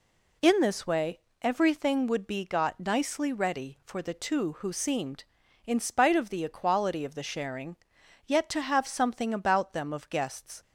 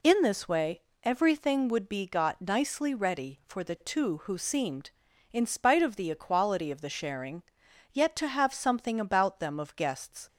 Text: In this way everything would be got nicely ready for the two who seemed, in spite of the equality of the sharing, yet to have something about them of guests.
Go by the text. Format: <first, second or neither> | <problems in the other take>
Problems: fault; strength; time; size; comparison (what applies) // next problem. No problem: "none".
neither | pauses between "way" and "everything"; slight; the same in both